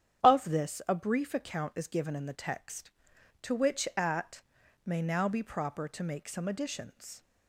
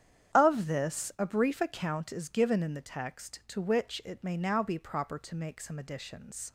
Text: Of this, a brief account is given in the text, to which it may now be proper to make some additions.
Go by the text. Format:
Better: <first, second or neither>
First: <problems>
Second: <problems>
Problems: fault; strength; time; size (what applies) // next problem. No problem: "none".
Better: second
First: starts louder than the rest; strong; until 1.2 s; 9 dB // says "at" for "it"; at 3.9 s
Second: starts louder than the rest; strong; until 1.4 s; 9.5 dB